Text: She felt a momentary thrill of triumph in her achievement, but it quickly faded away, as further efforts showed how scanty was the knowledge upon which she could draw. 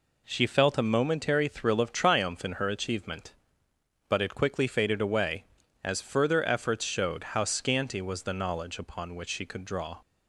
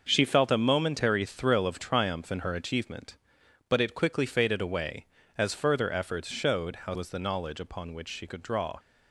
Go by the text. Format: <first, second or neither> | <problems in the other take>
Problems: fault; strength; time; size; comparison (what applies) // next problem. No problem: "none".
first | starts louder than the rest; noticeable; until 1.0 s; 6 dB // skips "scanty"; at 6.9 s